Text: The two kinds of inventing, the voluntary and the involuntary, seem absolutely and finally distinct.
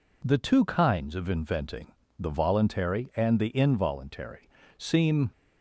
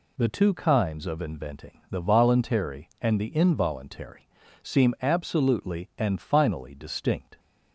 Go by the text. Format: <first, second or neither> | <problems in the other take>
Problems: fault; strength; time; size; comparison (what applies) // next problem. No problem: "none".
second | stops before "absolutely and finally distinct"; at 5.3 s